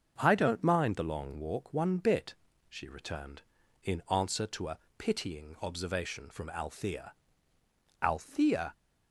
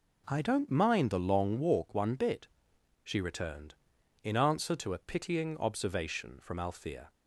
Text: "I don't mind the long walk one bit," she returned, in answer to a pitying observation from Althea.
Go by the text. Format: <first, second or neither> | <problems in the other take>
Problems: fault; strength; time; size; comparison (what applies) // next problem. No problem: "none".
second | starts louder than the rest; until 1.1 s; 6.5 dB // pauses between "a" and "pitying"; slight; at 4.7 s; 0.18 s long // says "Althea" twice; at 8.0 s